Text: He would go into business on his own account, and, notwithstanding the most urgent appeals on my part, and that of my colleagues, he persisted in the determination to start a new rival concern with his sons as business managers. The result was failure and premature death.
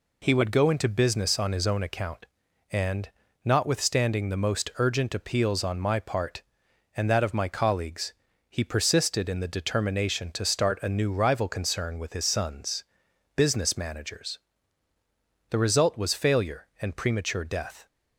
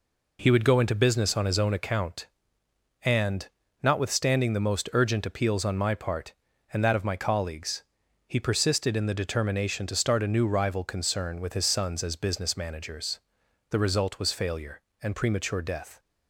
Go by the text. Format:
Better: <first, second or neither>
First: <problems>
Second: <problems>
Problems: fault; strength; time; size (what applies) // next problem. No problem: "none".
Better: second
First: skips "as"; at 13.0 s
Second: none